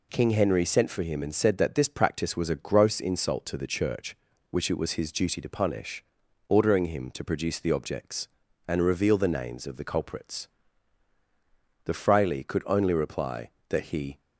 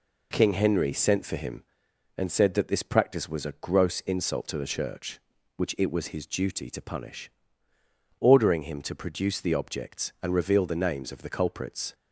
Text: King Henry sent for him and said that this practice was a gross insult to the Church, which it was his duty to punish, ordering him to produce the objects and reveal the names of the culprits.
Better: second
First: goes on to say "The fraile could only reply that he"; strong; from 11.8 s on; 2.3 s long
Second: none

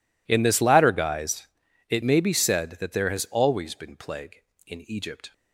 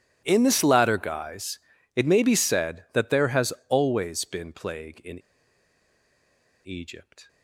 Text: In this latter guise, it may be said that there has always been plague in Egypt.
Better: first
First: none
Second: pauses between "has" and "always"; slight; at 3.5 s; 0.16 s long // pauses between "in" and "Egypt"; strong; at 5.1 s; 1.4 s long

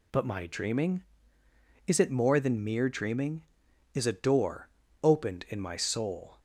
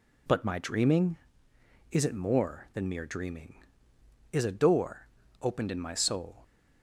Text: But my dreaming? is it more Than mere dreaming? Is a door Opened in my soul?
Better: neither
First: pauses between "door" and "Opened"; slight; at 4.6 s; 0.36 s long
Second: pauses between "door" and "Opened"; slight; at 5.0 s; 0.34 s long

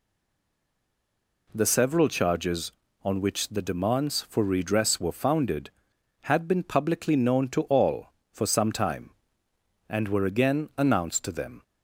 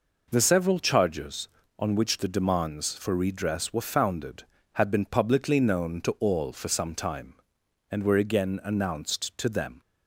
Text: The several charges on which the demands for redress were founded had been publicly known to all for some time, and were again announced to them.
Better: second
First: stays silent before the first word; noticeable; until 1.4 s; 1.4 s long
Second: none

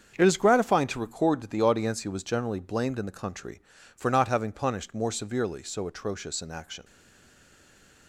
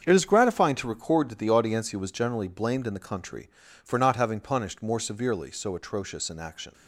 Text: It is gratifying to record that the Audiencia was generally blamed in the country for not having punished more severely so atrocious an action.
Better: second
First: starts louder than the rest; strong; until 1.1 s; 7 dB // stays silent after the last word; noticeable; from 6.8 s on; 1.2 s long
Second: starts louder than the rest; strong; until 1.0 s; 7 dB

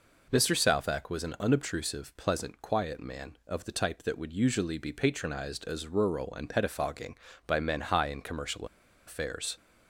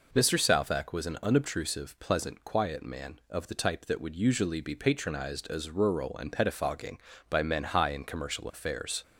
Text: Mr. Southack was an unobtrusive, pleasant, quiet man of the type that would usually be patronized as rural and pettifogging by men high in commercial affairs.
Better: second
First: pauses between "commercial" and "affairs"; at 8.6 s; 0.41 s long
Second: none

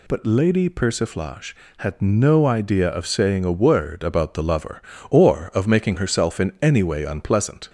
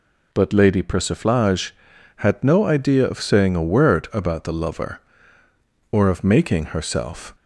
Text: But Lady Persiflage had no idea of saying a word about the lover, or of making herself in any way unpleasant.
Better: first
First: none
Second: stops before "in any way unpleasant"; at 7.3 s

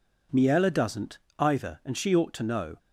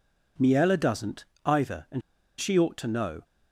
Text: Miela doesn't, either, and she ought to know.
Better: first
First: none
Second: pauses between "and" and "she"; at 2.0 s; 0.38 s long

